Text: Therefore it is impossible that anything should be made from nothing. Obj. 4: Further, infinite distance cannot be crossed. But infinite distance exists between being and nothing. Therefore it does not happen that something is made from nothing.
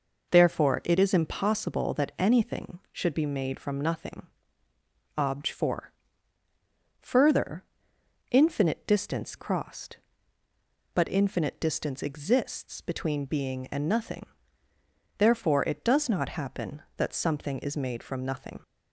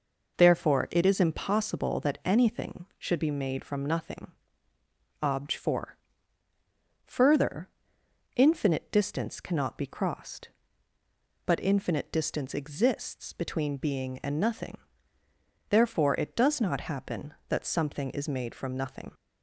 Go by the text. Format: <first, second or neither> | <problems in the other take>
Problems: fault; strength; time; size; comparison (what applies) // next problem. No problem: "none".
second | skips "cannot be"; at 9.3 s